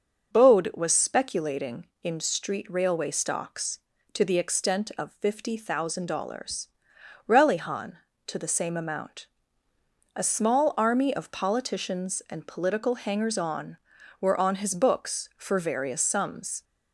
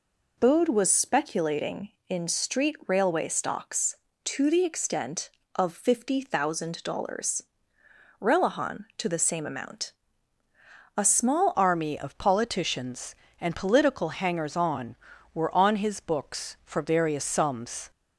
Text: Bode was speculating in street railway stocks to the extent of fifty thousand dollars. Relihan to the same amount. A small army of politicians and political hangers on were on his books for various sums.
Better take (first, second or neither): first